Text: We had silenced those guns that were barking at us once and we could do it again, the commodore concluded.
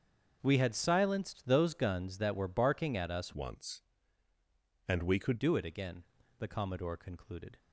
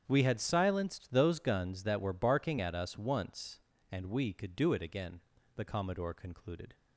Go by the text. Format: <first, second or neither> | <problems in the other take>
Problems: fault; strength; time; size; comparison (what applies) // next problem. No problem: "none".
second | starts louder than the rest; until 1.4 s; 7 dB; strong in the second // changes voice from "once" to "could"; from 3.3 to 5.4 s; 2.1 s long